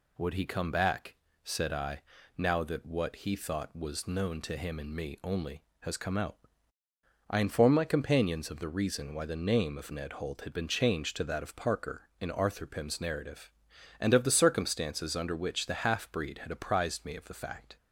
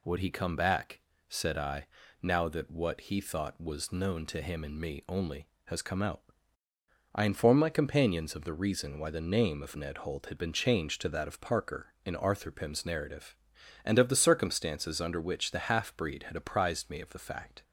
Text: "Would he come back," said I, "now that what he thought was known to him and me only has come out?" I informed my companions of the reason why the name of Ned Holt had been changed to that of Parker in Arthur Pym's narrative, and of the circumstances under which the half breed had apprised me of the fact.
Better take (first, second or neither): neither